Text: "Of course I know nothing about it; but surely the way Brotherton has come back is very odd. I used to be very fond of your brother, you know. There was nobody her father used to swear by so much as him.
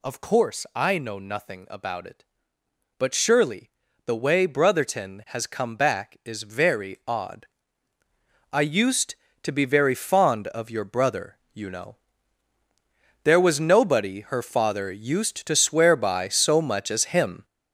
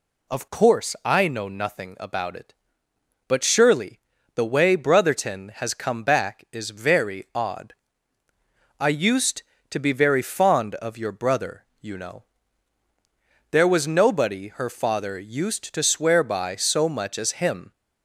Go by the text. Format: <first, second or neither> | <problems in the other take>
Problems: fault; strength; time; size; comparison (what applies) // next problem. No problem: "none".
second | gets louder; throughout; 7 dB // pauses between "surely" and "the"; at 3.6 s; 0.38 s long; also in the second